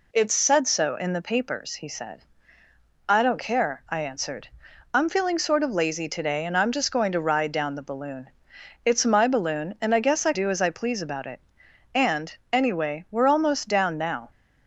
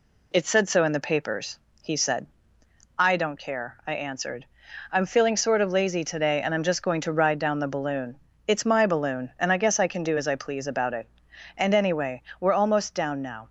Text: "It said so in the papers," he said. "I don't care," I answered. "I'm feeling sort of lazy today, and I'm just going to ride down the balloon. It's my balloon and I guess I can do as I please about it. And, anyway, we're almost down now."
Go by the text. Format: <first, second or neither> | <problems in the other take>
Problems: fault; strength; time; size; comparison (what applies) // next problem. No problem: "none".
second | skips "can"; at 10.3 s